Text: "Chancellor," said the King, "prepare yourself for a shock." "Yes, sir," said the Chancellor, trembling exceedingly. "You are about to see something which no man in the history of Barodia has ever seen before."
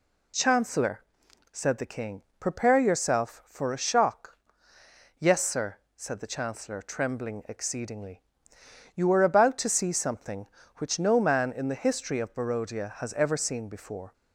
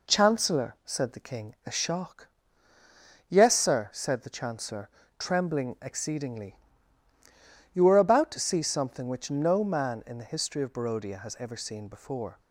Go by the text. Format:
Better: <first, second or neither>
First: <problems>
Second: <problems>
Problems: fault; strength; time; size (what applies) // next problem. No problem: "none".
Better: first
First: none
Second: skips "prepare yourself for"; at 1.5 s